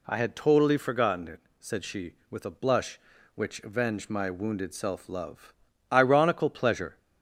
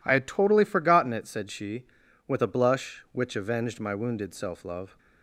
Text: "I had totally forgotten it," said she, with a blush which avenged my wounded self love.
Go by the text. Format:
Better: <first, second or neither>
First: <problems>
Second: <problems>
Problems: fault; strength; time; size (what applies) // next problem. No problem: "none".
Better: second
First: goes on to say "Ironical pleasure"; noticeable; from 5.8 s on; 1.0 s long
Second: none